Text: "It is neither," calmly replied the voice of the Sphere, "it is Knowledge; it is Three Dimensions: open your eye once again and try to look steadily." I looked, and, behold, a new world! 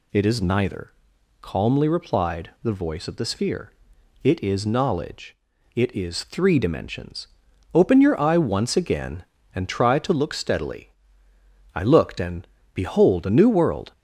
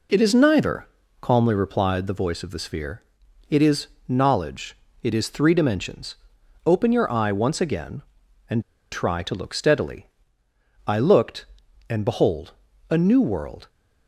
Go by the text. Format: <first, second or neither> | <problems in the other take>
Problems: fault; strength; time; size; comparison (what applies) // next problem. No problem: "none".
first | pauses between "is" and "Knowledge"; slight; at 3.8 s; 0.22 s long // pauses between "and" and "try"; slight; at 8.6 s; 0.31 s long